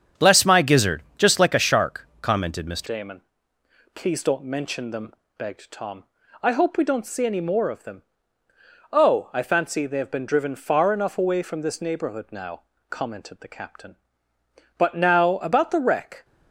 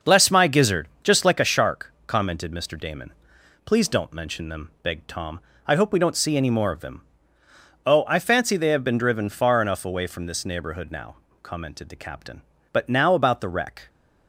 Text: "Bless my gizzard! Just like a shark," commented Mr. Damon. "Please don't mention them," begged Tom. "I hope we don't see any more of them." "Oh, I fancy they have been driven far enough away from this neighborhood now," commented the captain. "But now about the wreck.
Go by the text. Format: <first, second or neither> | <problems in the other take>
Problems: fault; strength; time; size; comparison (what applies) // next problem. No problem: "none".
second | starts louder than the rest; strong; until 1.3 s; 8 dB; noticeable in the second // changes voice at "Damon"; from 2.8 s on; 13.4 s long